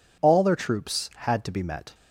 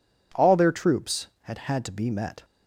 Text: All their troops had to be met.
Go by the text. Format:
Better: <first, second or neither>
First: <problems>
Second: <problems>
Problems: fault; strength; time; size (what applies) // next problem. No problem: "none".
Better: first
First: none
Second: says "had" twice; at 1.5 s